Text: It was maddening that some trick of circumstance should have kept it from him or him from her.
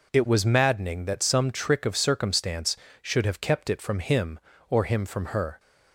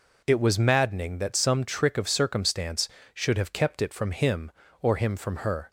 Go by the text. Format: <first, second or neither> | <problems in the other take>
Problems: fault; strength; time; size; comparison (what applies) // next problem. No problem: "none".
neither | none